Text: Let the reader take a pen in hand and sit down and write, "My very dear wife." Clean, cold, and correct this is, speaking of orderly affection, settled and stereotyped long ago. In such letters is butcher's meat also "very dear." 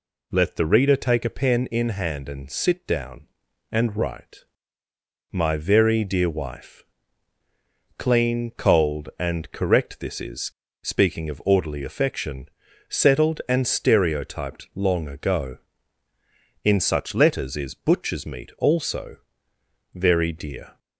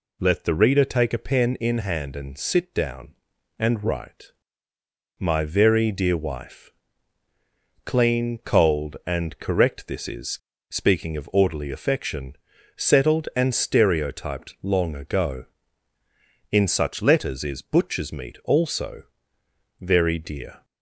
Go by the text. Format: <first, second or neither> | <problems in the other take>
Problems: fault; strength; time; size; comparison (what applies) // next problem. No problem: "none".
neither | pauses between "also" and "very"; noticeable; the same in both